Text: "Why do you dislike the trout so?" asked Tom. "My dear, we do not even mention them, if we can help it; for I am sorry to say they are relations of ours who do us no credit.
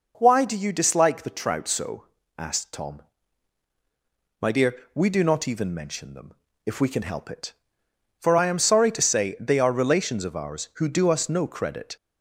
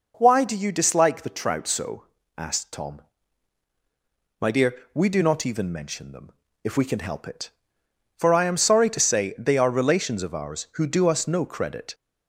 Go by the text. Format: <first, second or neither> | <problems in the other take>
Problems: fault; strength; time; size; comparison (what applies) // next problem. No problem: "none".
neither | none